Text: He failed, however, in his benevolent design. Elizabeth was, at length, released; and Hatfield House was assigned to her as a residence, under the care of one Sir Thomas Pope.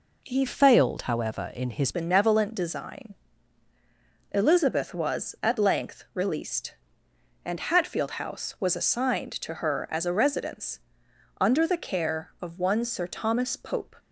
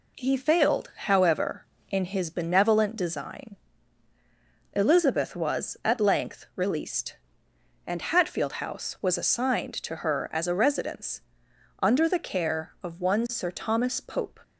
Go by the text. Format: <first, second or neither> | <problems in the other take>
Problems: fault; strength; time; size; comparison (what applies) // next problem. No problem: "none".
second | changes voice from "failed" to "his"; from 0.4 to 1.9 s; 1.5 s long